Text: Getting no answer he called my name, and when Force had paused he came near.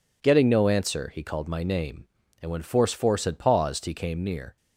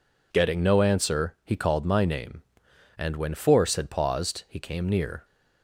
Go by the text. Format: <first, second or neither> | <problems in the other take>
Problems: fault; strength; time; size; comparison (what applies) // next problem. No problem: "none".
second | says "Force" twice; at 2.9 s